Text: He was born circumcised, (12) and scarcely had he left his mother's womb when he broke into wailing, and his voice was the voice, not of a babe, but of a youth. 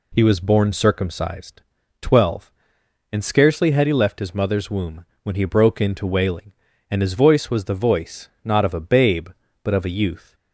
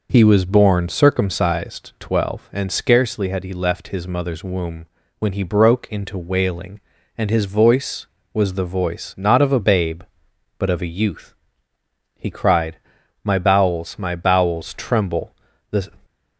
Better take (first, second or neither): first